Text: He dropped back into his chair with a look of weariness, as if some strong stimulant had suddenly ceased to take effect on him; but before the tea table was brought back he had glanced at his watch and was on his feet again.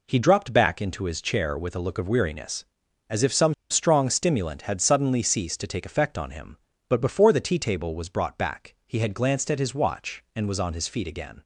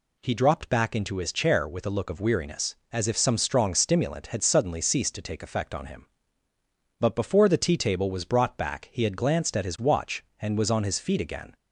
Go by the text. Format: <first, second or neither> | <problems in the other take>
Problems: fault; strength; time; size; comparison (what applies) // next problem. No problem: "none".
second | pauses between "some" and "strong"; slight; at 3.5 s; 0.16 s long